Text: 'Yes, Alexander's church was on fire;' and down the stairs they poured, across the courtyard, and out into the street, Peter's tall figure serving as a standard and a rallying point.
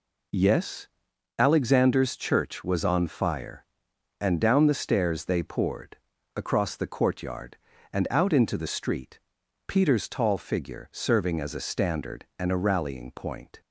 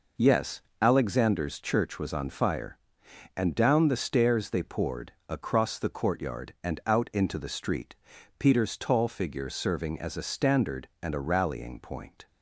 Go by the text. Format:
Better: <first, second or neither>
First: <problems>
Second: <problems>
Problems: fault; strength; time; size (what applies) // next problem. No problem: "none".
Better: neither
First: none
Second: none